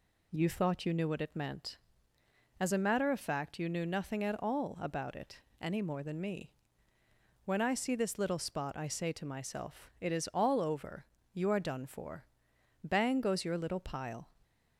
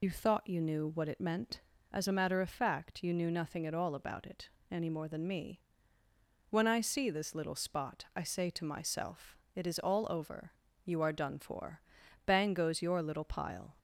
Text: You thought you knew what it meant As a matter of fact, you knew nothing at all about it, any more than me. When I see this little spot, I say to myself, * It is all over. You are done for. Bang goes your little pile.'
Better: first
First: none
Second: loses the start of "You"; at 0.0 s; 25 ms

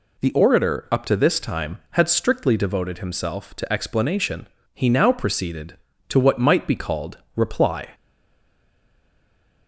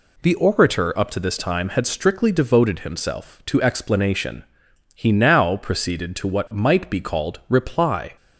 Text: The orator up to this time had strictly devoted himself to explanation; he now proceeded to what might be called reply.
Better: second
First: pauses between "called" and "reply"; slight; at 7.1 s; 0.18 s long // stays silent after the last word; noticeable; from 7.9 s on; 1.7 s long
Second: none

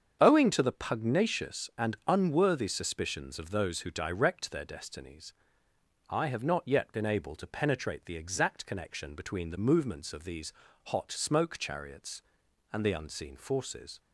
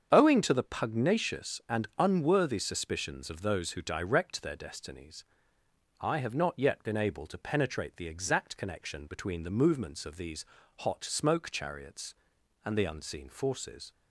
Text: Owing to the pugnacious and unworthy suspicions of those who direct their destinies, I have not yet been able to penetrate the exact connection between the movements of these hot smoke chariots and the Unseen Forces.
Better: neither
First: starts louder than the rest; strong; until 1.2 s; 7.5 dB // pauses between "these" and "hot"; slight; at 10.5 s; 0.32 s long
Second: starts louder than the rest; strong; until 1.1 s; 7.5 dB // pauses between "these" and "hot"; slight; at 10.4 s; 0.32 s long

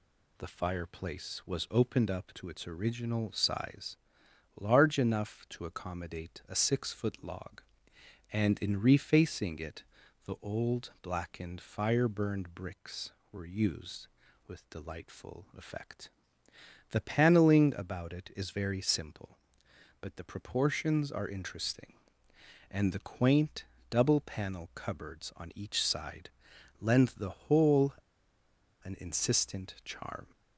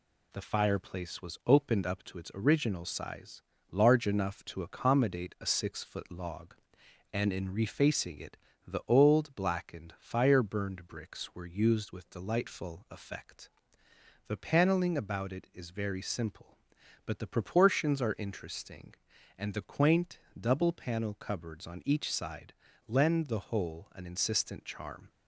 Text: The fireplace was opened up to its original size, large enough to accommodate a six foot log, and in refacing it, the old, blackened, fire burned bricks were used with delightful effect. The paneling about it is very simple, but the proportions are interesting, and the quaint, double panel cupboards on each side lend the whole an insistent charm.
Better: second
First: pauses between "side" and "lend"; noticeable; at 26.2 s; 0.50 s long // pauses between "whole" and "an"; noticeable; at 27.9 s; 0.88 s long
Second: pauses between "side" and "lend"; slight; at 22.5 s; 0.34 s long

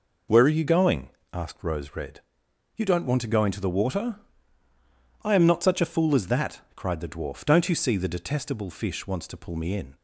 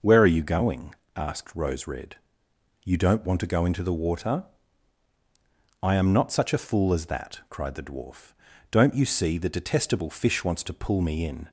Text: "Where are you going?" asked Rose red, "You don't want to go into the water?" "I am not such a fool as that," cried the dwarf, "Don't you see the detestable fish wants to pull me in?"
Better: neither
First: none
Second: none

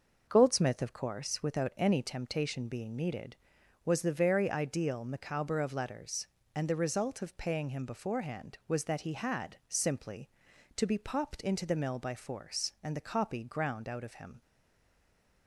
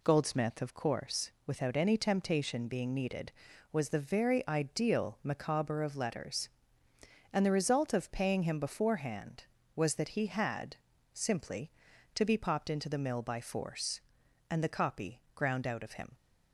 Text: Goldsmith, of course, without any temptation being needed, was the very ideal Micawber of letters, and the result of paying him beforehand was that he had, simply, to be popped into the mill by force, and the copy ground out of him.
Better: second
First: stays silent after the last word; from 14.4 s on; 1.0 s long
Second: none

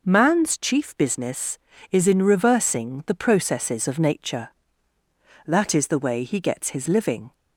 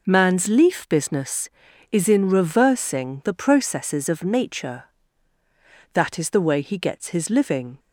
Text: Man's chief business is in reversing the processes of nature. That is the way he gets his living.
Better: first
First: none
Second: says "leaf" for "chief"; at 0.4 s

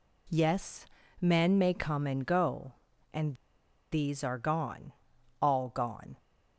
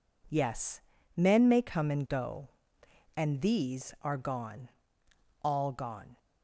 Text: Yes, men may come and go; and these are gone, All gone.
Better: second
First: pauses between "and" and "these"; noticeable; at 3.3 s; 0.58 s long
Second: none

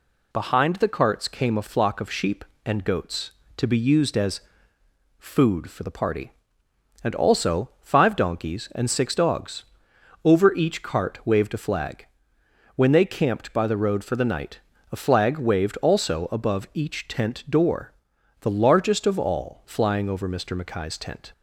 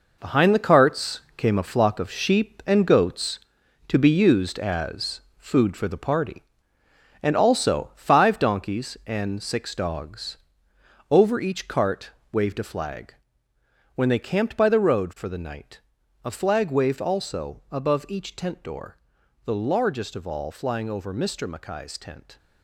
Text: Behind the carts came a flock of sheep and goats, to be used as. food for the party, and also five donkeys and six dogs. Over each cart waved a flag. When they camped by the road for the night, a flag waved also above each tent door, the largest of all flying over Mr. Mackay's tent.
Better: first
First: none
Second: gets quieter; strong; throughout; 9.5 dB // pauses between "carts" and "came"; slight; at 1.2 s; 0.16 s long // pauses between "cart" and "waved"; slight; at 12.1 s; 0.22 s long

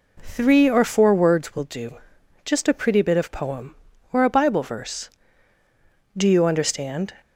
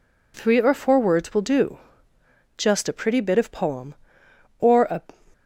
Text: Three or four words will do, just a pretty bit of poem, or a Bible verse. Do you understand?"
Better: first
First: none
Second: stops before "Bible verse Do you understand"; at 5.3 s

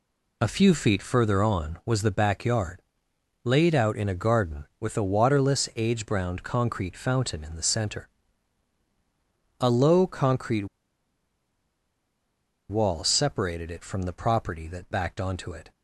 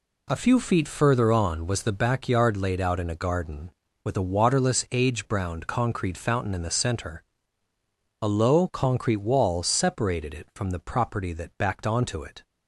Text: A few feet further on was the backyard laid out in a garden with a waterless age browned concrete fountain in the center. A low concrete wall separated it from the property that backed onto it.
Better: second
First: pauses between "backyard" and "laid"; noticeable; at 2.8 s; 0.64 s long // pauses between "concrete" and "wall"; strong; at 10.6 s; 2.0 s long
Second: none

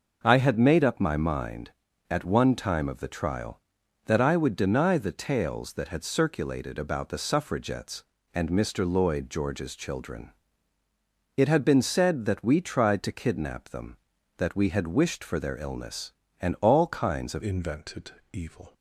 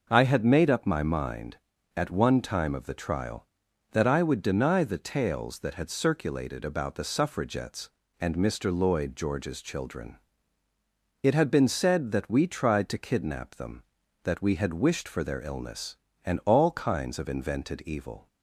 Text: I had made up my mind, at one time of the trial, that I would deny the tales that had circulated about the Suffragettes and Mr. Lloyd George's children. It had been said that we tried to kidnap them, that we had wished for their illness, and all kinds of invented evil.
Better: second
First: changes voice at "invented"; from 17.4 s on; 1.3 s long // pauses between "invented" and "evil"; slight; at 18.1 s; 0.20 s long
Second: none

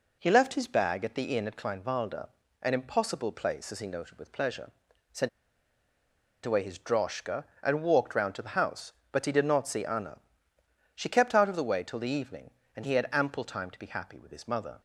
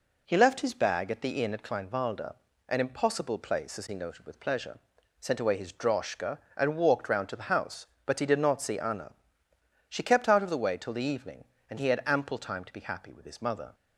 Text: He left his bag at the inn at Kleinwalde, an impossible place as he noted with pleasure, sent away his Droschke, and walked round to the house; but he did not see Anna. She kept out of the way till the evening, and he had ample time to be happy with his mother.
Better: second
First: pauses between "sent" and "away"; at 5.2 s; 1.1 s long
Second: none

